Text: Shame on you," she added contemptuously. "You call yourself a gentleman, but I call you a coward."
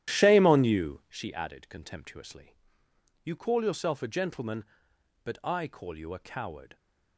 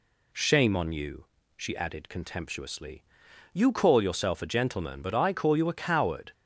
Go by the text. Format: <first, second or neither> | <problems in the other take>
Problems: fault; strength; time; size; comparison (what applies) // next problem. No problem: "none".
second | starts louder than the rest; strong; until 1.2 s; 11.5 dB